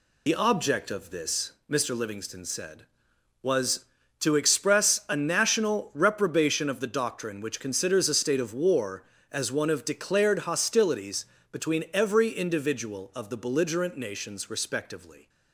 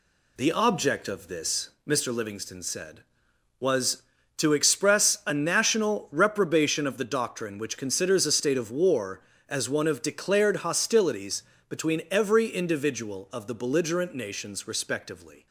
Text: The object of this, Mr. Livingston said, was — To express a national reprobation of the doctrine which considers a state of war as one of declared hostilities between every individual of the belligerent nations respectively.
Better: second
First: loses the start of "The"; at 0.2 s; 55 ms // pauses between "hostilities" and "between"; slight; at 11.2 s; 0.28 s long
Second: pauses between "hostilities" and "between"; slight; at 11.4 s; 0.28 s long

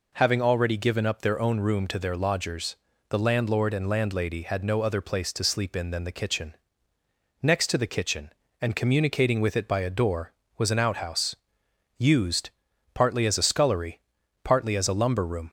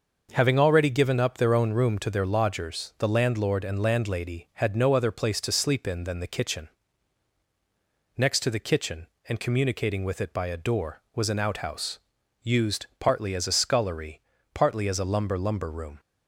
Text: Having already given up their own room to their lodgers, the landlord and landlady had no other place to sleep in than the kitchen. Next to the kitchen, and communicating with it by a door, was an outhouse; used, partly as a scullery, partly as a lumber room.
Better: first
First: none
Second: starts louder than the rest; noticeable; until 1.3 s; 6 dB // says "lumber" twice; at 15.3 s

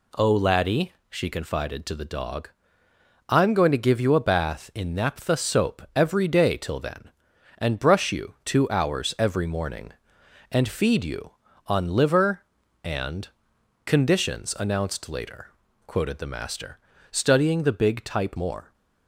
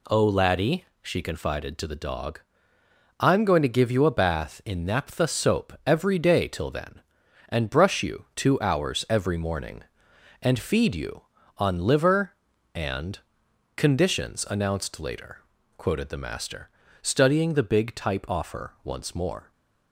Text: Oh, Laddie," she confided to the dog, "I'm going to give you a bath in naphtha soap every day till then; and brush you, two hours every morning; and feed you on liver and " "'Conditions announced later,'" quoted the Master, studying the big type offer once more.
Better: second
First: skips "offer once"; at 18.3 s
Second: none

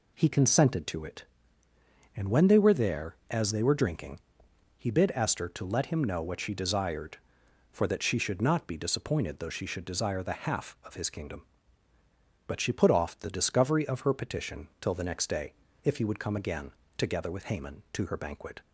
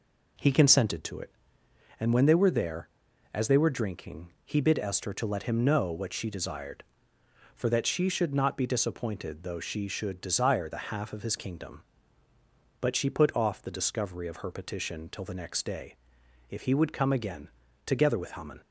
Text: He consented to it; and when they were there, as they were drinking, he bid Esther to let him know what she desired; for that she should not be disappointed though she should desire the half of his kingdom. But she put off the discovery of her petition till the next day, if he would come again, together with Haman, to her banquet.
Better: first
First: none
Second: stops before "to her banquet"; at 18.6 s

